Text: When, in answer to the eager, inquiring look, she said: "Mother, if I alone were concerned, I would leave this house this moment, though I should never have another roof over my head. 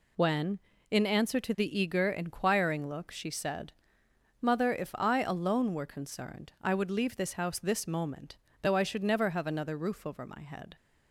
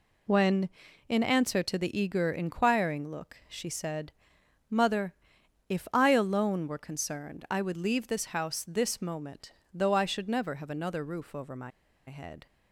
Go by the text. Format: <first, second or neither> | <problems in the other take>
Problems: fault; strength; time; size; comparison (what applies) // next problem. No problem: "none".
first | pauses between "my" and "head"; at 11.7 s; 0.37 s long